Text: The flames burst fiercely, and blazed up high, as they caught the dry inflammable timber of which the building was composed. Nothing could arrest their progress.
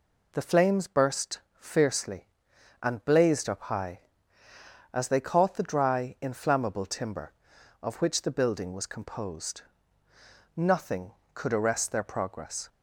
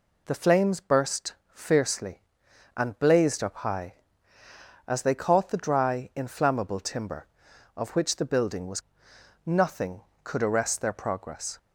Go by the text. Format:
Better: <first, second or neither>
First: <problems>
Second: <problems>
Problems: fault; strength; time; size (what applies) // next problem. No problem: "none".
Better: first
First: pauses between "burst" and "fiercely"; slight; at 1.3 s; 0.20 s long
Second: pauses between "burst" and "fiercely"; slight; at 1.3 s; 0.20 s long // skips "composed"; at 9.1 s